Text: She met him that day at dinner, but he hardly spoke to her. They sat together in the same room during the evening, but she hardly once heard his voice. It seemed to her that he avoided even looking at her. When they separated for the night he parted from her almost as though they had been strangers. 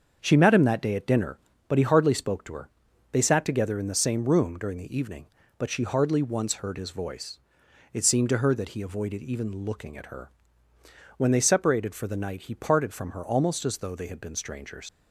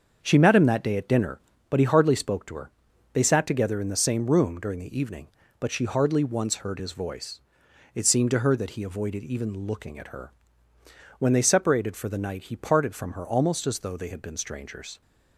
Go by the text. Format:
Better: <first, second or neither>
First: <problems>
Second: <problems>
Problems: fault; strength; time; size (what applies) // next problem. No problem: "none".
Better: second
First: starts louder than the rest; until 1.2 s; 7 dB // leaves "strangers" unfinished; at 14.8 s; 105 ms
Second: starts louder than the rest; until 1.2 s; 7 dB